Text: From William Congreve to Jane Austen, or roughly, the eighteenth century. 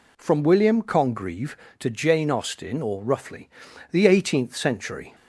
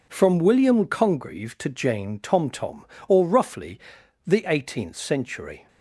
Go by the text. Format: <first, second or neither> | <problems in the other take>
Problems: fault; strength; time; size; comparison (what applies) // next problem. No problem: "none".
first | says "Tomtom" for "Austen"; at 2.1 s